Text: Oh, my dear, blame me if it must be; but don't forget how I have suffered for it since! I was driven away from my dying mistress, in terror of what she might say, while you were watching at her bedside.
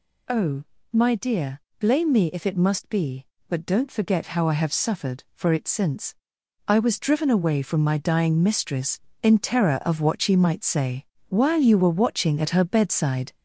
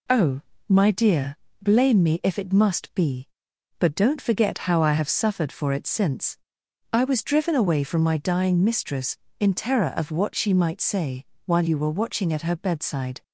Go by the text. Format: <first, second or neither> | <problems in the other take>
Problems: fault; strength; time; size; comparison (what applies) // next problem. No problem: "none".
second | gets louder; noticeable; throughout; 4 dB